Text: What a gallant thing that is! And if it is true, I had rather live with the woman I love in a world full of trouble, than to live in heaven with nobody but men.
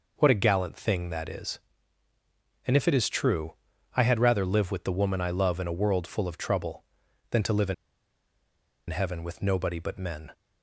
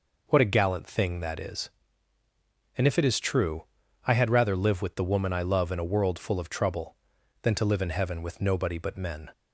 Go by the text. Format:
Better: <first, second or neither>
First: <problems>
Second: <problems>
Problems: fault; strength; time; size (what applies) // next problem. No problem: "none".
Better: second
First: pauses between "in" and "heaven"; at 7.7 s; 1.1 s long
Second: none